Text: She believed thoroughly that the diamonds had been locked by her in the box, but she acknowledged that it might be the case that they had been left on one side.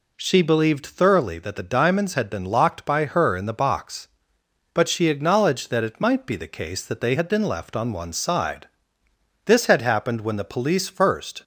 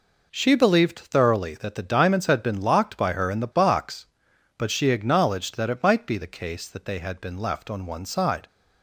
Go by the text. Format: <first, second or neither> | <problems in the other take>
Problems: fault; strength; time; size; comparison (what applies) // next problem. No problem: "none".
second | goes on to say "This had happened when the police first"; strong; from 9.4 s on; 1.9 s long